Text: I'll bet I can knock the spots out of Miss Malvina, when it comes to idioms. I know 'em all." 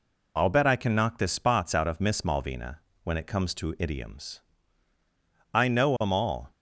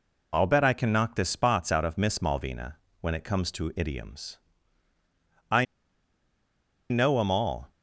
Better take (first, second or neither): first